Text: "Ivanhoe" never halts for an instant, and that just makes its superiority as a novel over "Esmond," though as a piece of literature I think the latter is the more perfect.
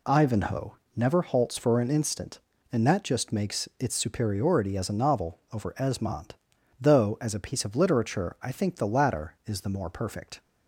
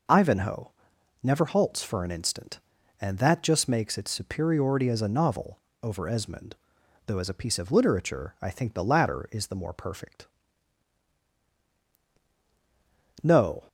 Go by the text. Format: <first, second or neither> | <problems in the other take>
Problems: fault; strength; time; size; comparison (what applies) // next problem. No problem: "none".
first | pauses between "Ivanhoe" and "never"; noticeable; at 0.7 s; 0.52 s long; slight in the first // pauses between "novel" and "over"; slight; at 5.5 s; 0.24 s long // goes on to say "No"; slight; from 13.2 s on; 0.42 s long